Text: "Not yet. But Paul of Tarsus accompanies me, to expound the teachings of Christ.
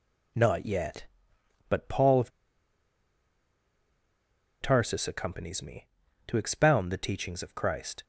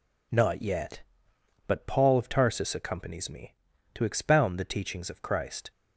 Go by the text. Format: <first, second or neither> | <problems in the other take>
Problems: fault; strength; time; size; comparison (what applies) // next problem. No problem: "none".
second | pauses between "of" and "Tarsus"; strong; at 2.3 s; 2.3 s long